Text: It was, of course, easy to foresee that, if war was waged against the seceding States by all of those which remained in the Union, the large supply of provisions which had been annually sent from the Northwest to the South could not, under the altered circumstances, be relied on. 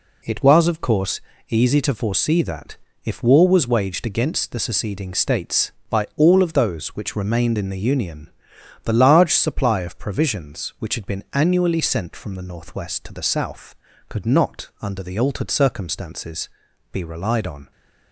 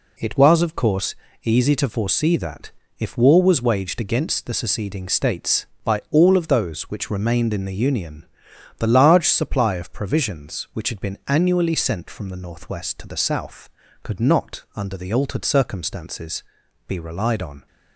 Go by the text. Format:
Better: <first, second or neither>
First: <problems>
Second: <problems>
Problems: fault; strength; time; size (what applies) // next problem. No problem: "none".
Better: neither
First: none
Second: none